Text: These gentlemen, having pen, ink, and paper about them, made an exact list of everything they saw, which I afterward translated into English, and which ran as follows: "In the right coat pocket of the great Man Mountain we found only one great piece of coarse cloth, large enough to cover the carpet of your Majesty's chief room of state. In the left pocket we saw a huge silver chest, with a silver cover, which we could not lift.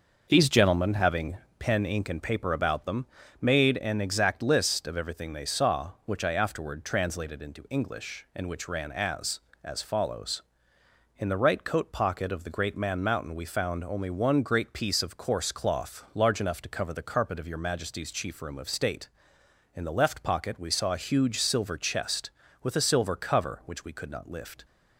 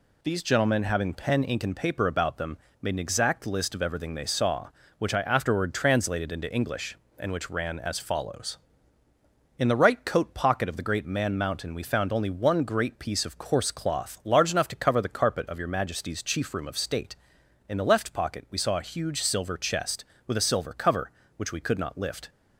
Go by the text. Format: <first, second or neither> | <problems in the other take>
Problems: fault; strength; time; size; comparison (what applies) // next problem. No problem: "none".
second | pauses between "having" and "pen"; slight; at 1.3 s; 0.20 s long // says "as" twice; at 9.6 s